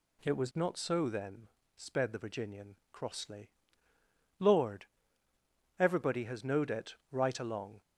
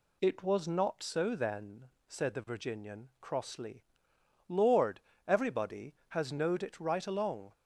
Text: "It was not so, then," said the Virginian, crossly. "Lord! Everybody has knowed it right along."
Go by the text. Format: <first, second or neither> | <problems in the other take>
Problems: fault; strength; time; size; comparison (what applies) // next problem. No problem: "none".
second | says "sped" for "said"; at 1.7 s // pauses between "it" and "right"; slight; at 6.9 s; 0.16 s long